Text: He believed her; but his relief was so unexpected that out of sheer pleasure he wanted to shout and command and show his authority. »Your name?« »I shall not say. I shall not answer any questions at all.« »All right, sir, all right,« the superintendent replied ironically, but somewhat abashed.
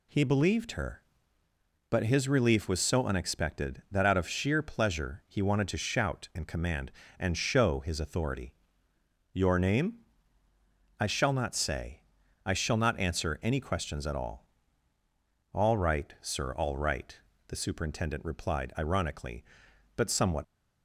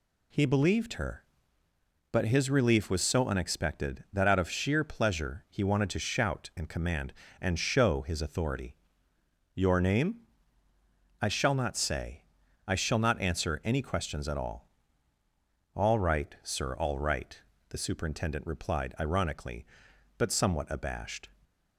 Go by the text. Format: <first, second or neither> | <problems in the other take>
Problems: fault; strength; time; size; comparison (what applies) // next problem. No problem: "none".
second | stops before "abashed"; at 20.4 s